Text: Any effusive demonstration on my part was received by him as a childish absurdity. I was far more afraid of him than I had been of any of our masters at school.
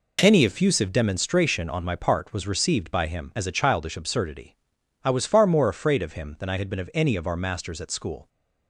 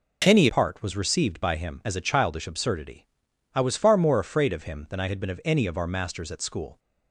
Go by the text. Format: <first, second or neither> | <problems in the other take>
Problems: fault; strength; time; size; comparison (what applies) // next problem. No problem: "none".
first | skips "effusive demonstration on my"; at 0.4 s